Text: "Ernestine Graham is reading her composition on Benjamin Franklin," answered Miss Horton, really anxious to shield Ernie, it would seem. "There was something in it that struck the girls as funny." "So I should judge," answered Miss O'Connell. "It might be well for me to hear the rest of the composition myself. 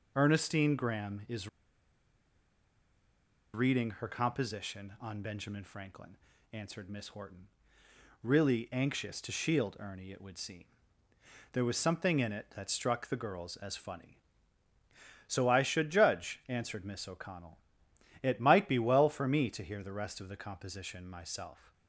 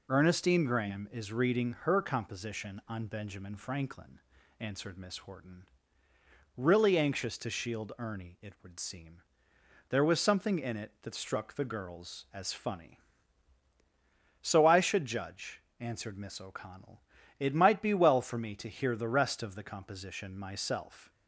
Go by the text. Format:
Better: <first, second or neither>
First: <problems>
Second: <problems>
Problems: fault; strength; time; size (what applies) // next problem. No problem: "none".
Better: second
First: pauses between "is" and "reading"; strong; at 1.4 s; 2.0 s long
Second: none